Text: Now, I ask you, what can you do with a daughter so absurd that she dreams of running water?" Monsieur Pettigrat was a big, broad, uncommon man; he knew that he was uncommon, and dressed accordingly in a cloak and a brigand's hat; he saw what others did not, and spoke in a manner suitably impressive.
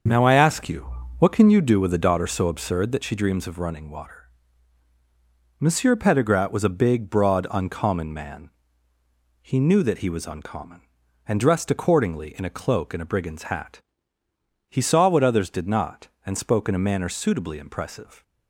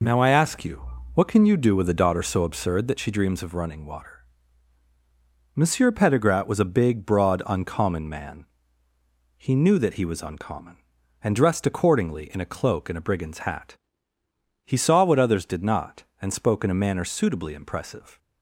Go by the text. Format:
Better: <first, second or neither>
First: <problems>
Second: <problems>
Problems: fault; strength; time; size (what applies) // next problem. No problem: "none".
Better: second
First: starts louder than the rest; until 1.8 s; 6.5 dB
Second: none